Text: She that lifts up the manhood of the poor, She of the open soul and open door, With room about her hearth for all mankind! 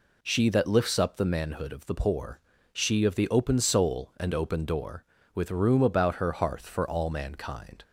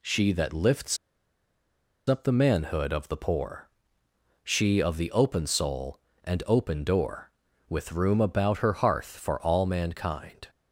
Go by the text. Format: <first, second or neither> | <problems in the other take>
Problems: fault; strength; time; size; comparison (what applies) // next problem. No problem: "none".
first | pauses between "lifts" and "up"; at 0.9 s; 1.1 s long